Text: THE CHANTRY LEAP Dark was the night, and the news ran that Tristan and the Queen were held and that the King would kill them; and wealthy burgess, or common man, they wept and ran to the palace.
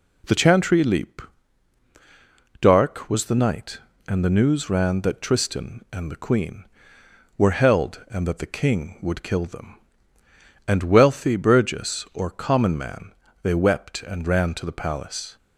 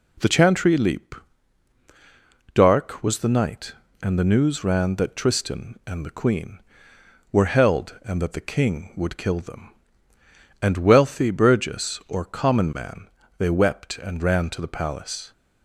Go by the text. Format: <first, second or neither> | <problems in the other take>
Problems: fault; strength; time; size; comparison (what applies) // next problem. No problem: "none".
neither | pauses between "LEAP" and "Dark"; strong; the same in both